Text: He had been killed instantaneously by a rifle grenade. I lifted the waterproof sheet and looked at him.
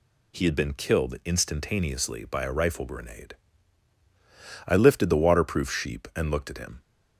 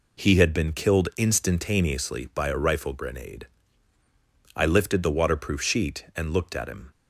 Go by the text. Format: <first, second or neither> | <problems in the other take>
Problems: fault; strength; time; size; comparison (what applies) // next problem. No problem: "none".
second | says "sheep" for "sheet"; at 5.7 s